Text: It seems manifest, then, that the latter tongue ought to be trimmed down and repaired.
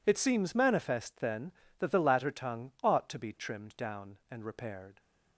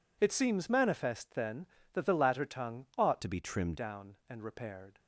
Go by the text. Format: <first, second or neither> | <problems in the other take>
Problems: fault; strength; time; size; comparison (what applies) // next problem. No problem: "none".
first | changes voice from "to" to "trimmed"; from 3.2 to 3.7 s; 0.5 s long